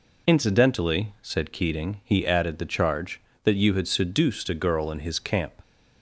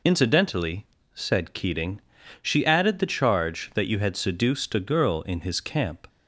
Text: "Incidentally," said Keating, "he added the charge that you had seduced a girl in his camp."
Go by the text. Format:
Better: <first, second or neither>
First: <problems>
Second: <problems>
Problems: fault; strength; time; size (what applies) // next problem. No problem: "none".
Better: first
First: none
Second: says "she" for "he"; at 2.4 s